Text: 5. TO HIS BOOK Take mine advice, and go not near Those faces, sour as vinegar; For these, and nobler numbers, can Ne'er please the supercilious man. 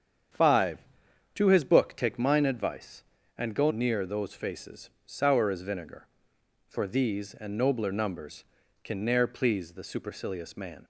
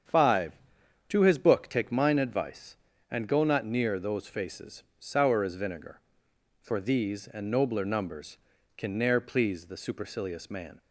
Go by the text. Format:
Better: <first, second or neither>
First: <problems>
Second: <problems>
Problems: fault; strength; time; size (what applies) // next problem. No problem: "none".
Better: second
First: starts louder than the rest; strong; until 1.8 s; 8 dB // skips "not"; at 3.7 s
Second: starts louder than the rest; strong; until 1.6 s; 8 dB